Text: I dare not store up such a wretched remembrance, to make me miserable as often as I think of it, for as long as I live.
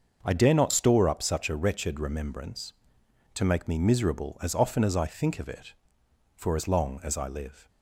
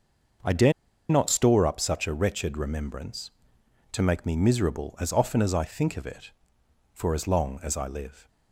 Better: first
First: starts louder than the rest; until 1.2 s; 6 dB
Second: starts louder than the rest; noticeable; until 1.8 s; 6 dB // pauses between "dare" and "not"; at 0.7 s; 0.37 s long

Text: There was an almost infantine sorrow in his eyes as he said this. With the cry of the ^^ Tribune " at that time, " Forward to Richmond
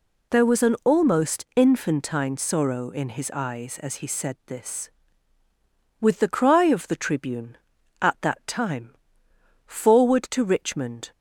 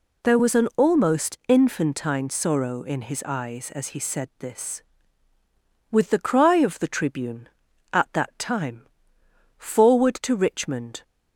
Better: neither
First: none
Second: none

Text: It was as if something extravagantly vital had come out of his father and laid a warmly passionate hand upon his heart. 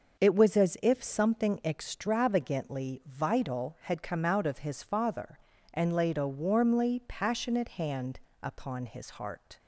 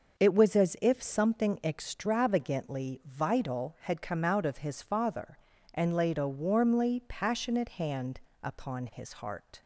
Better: neither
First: starts louder than the rest; until 1.2 s; 6 dB // pauses between "hand" and "upon"; slight; at 8.2 s; 0.22 s long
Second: starts louder than the rest; until 1.2 s; 6 dB // pauses between "hand" and "upon"; slight; at 8.2 s; 0.22 s long

